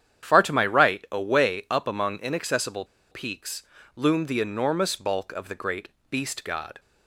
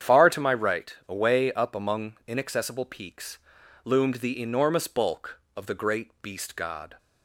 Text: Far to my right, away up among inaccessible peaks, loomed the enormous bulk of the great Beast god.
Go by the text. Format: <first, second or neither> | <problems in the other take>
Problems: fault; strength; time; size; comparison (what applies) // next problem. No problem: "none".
second | starts louder than the rest; strong; until 1.3 s; 9 dB; strong in the second // pauses between "inaccessible" and "peaks"; slight; at 2.8 s; 0.25 s long // pauses between "great" and "Beast"; slight; at 5.8 s; 0.20 s long